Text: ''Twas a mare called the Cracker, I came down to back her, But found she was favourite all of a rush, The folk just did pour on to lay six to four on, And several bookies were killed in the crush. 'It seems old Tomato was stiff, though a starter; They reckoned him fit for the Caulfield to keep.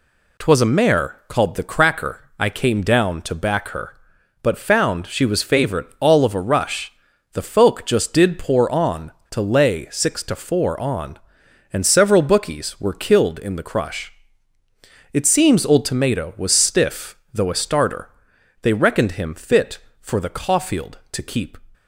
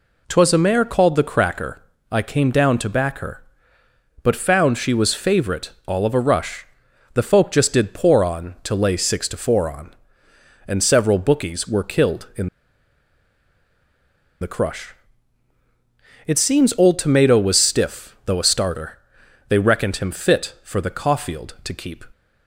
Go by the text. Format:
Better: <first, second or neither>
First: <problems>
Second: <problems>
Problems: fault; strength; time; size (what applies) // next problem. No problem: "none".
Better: first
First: none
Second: pauses between "favourite" and "all"; slight; at 5.7 s; 0.16 s long // pauses between "in" and "the"; strong; at 12.4 s; 1.9 s long